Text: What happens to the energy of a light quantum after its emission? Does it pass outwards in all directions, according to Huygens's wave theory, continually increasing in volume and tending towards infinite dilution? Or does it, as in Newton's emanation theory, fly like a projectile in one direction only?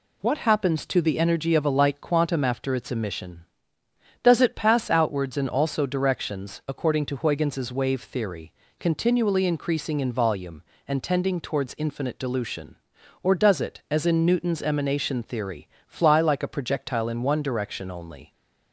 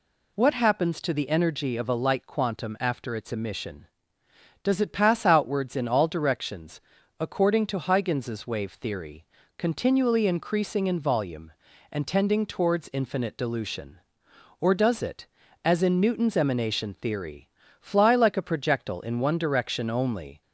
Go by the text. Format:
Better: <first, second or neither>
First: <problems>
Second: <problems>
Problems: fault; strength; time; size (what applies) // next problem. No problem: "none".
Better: second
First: says "also" for "all"; at 5.4 s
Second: none